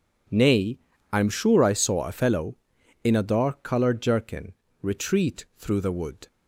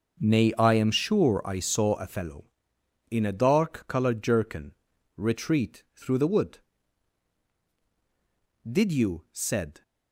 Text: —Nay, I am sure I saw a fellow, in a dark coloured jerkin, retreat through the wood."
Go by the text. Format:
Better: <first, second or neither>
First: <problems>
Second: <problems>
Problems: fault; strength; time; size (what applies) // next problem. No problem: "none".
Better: first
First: none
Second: starts louder than the rest; noticeable; until 1.2 s; 6 dB // goes on to say "Did you said"; noticeable; from 8.6 s on; 1.1 s long